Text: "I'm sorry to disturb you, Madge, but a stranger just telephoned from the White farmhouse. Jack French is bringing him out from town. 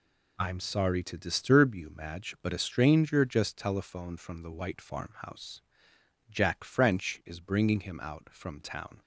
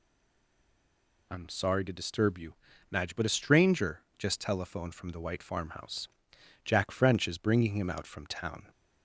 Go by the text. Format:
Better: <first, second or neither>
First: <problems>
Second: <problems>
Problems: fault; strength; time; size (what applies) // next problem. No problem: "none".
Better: first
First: none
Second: stays silent before the first word; noticeable; until 1.3 s; 1.3 s long // pauses between "stranger" and "just"; slight; at 4.0 s; 0.16 s long